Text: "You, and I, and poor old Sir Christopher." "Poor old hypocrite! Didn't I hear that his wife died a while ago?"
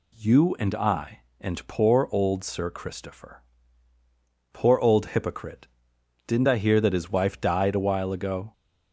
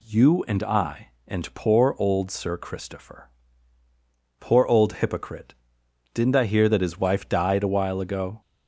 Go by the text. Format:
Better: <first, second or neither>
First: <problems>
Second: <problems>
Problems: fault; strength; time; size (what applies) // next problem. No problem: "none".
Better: neither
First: none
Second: none